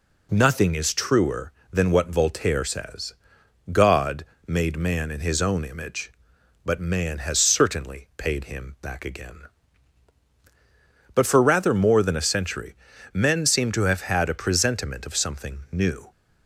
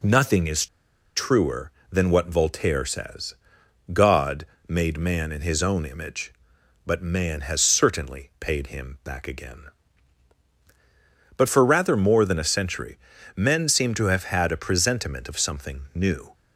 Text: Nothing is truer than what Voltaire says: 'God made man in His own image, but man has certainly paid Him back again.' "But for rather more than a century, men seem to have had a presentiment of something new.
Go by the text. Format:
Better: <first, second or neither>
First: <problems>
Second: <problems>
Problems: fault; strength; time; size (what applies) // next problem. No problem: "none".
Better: first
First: pauses between "God" and "made"; slight; at 4.2 s; 0.20 s long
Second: pauses between "is" and "truer"; noticeable; at 0.6 s; 0.49 s long // pauses between "God" and "made"; slight; at 4.4 s; 0.20 s long